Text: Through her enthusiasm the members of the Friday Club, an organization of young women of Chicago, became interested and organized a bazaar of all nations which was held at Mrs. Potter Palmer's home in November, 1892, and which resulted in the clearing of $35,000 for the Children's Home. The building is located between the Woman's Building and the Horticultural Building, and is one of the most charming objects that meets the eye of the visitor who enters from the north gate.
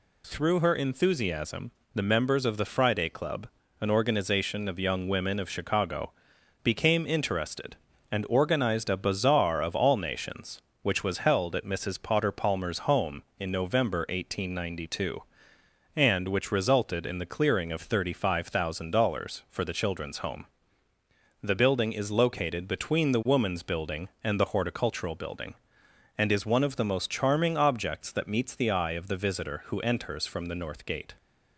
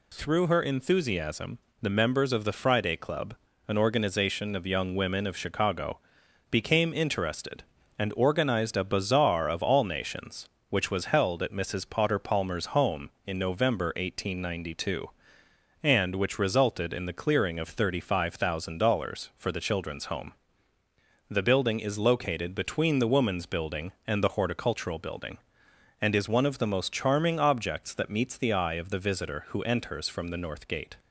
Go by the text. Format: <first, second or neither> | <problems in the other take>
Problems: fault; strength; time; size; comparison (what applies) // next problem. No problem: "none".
neither | pauses between "enthusiasm" and "the"; slight; the same in both